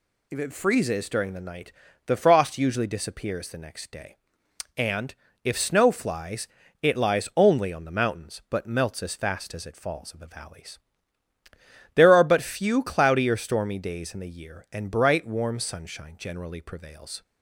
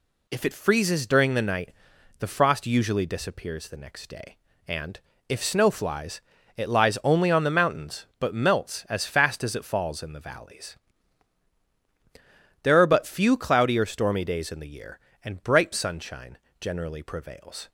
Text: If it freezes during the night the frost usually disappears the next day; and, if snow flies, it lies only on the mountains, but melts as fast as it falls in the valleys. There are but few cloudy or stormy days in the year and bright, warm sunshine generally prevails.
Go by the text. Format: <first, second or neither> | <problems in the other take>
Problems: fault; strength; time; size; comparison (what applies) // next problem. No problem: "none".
first | pauses between "night" and "the"; noticeable; at 1.7 s; 0.46 s long; slight in the first // skips "warm"; at 15.7 s // pauses between "sunshine" and "generally"; slight; at 16.3 s; 0.22 s long